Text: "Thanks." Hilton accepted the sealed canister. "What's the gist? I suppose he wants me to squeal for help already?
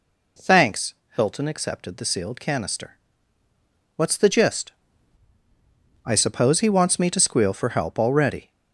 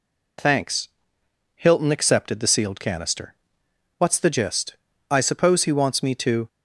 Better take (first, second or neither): first